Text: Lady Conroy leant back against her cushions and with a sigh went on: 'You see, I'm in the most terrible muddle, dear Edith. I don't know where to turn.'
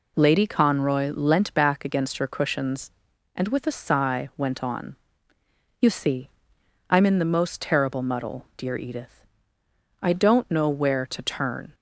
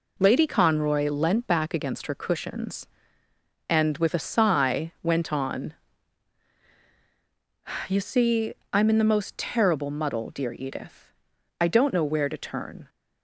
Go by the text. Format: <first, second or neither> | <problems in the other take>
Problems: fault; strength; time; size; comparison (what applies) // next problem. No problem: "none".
neither | none